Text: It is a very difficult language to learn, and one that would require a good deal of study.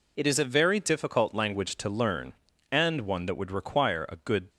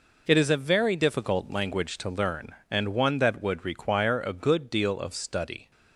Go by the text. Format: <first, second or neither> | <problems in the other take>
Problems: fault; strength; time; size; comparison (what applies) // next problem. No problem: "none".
second | stops before "deal of study"; at 4.5 s